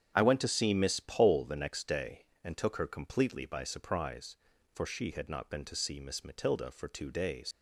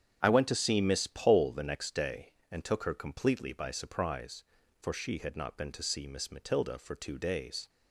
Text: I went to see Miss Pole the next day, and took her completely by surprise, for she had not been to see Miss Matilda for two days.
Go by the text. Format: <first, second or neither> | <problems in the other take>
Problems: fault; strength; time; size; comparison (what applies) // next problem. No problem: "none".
second | starts louder than the rest; strong; until 1.1 s; 8 dB; strong in the second // leaves "days" unfinished; at 7.5 s; 100 ms